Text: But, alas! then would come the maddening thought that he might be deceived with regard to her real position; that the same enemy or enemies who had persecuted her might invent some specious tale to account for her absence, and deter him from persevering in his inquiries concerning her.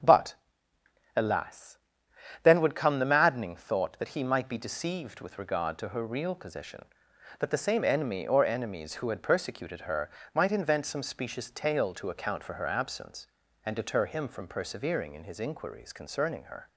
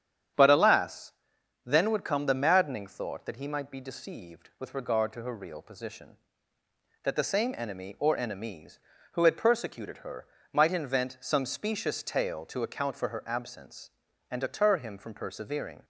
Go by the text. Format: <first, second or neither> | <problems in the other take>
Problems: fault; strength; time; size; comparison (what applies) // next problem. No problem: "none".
first | starts louder than the rest; strong; until 1.8 s; 9.5 dB; strong in the first // pauses between "her" and "might"; slight; at 10.2 s; 0.26 s long; slight in the first // stops before "in his inquiries concerning her"; at 15.8 s